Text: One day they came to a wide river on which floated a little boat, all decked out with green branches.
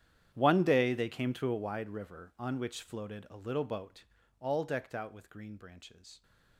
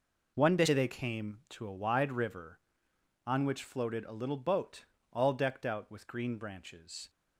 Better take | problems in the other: second | gets quieter; strong; throughout; 21 dB

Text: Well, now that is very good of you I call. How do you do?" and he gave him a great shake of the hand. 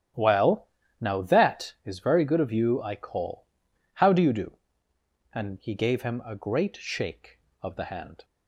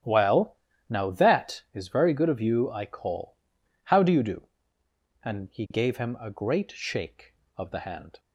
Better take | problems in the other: neither | starts louder than the rest; strong; the same in both

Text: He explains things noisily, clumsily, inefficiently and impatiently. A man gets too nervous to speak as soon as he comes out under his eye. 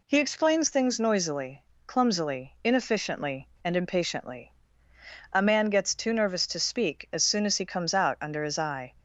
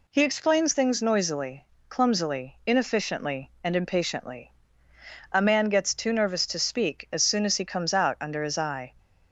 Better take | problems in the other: neither | none

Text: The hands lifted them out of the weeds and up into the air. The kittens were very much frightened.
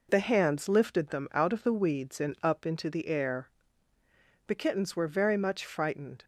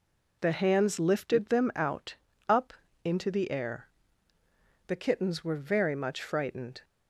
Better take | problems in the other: first | skips "of the weeds and"; at 2.3 s // pauses between "up" and "into"; slight; at 2.7 s; 0.32 s long

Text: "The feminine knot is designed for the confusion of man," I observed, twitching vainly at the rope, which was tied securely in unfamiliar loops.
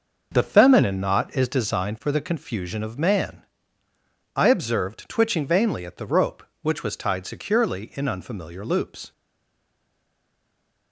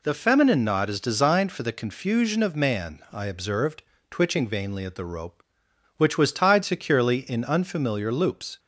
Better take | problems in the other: second | stays silent after the last word; noticeable; from 9.1 s on; 1.8 s long

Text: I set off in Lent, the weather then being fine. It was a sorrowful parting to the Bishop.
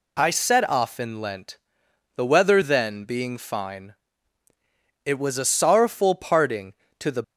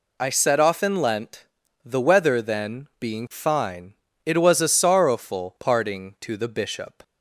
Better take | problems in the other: second | stops before "Bishop"; at 7.2 s

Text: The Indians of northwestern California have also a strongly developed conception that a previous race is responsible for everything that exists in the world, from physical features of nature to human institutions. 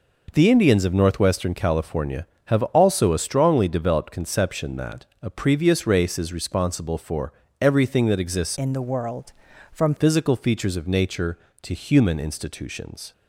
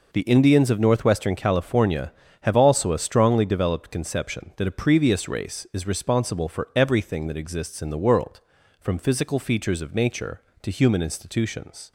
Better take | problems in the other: second | pauses between "that" and "a"; slight; at 5.0 s; 0.18 s long // pauses between "for" and "everything"; slight; at 7.3 s; 0.26 s long // changes voice from "in" to "from"; from 8.5 to 9.9 s; 1.4 s long

